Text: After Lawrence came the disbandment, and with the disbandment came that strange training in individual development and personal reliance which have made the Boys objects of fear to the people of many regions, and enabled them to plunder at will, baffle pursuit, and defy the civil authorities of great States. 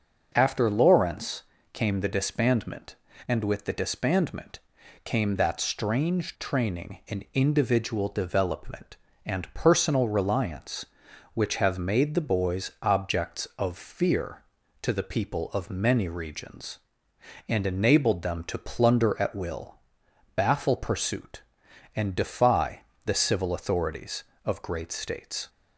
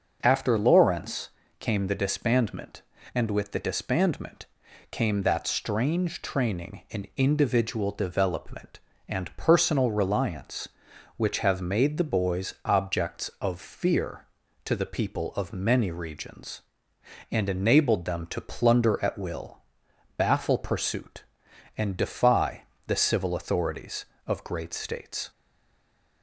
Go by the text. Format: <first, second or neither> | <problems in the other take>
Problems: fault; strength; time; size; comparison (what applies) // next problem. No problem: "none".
first | starts louder than the rest; noticeable; until 1.2 s; 6 dB; noticeable in the first // pauses between "Lawrence" and "came"; slight; at 1.2 s; 0.30 s long; slight in the first // pauses between "disbandment" and "came"; noticeable; at 4.4 s; 0.48 s long; noticeable in the first // pauses between "defy" and "the"; slight; at 22.6 s; 0.24 s long; slight in the first // stays silent after the last word; slight; from 25.3 s on; 0.9 s long